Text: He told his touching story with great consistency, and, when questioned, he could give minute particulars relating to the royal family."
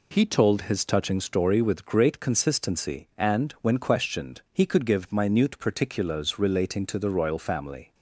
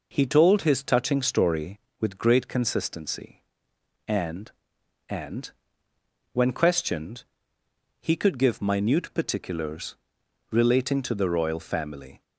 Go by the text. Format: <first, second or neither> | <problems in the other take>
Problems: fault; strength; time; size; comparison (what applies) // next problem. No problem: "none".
first | says "and" twice; at 5.0 s // pauses between "particulars" and "relating"; noticeable; at 9.9 s; 0.54 s long